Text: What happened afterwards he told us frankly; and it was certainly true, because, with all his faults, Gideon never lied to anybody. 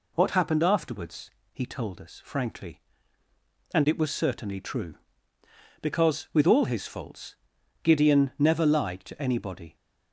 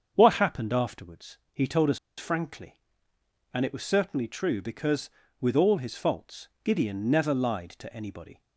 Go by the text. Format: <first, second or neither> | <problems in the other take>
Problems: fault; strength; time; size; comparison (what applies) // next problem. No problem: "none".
first | starts louder than the rest; until 1.1 s; 7 dB // pauses between "afterwards" and "he"; slight; at 1.3 s; 0.16 s long; slight in the first // pauses between "us" and "frankly"; slight; at 1.9 s; 0.19 s long